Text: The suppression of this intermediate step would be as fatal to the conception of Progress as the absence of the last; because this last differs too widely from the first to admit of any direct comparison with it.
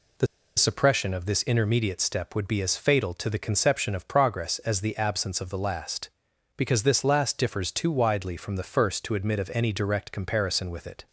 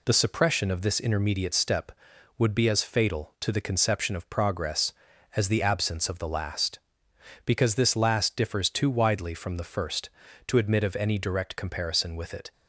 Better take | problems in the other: second | pauses between "The" and "suppression"; slight; at 0.2 s; 0.32 s long

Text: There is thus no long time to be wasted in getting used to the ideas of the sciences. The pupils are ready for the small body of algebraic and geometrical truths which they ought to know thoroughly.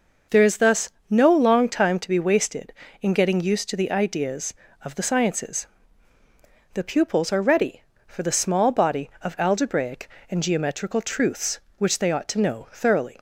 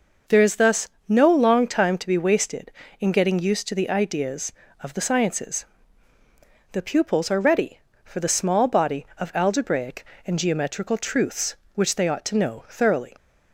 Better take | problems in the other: neither | pauses between "thus" and "no"; slight; the same in both

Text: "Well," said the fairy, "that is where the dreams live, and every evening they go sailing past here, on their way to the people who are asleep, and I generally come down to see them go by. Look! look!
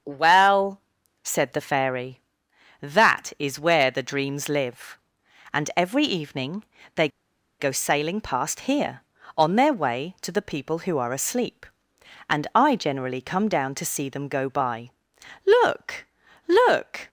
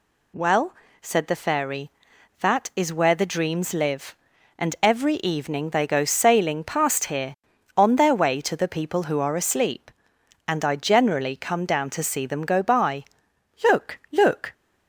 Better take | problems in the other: second | starts louder than the rest; strong; until 1.4 s; 7.5 dB // pauses between "evening" and "they"; slight; at 6.6 s; 0.30 s long // pauses between "they" and "go"; noticeable; at 7.0 s; 0.51 s long

